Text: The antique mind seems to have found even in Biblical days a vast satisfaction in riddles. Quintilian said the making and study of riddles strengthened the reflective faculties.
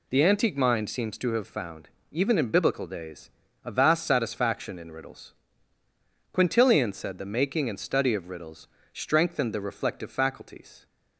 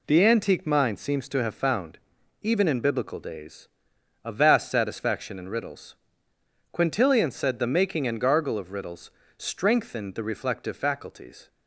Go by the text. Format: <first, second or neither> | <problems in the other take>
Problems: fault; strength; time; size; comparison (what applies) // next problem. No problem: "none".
first | pauses between "found" and "even"; noticeable; at 1.9 s; 0.46 s long; slight in the first // pauses between "days" and "a"; noticeable; at 3.6 s; 0.54 s long; slight in the first // says "gargle" for "study"; at 8.2 s // pauses between "riddles" and "strengthened"; slight; at 9.1 s; 0.28 s long; slight in the first